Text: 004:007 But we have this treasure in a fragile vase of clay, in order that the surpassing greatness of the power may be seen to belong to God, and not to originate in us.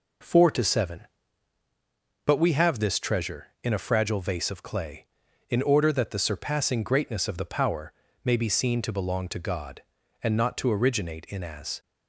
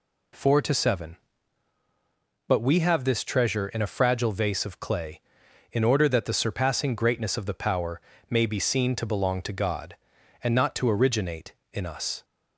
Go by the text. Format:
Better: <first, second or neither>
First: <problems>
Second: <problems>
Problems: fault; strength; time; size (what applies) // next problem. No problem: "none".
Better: second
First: pauses between "power" and "may"; slight; at 7.9 s; 0.32 s long // says "as" for "us"; at 11.4 s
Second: pauses between "power" and "may"; slight; at 7.9 s; 0.28 s long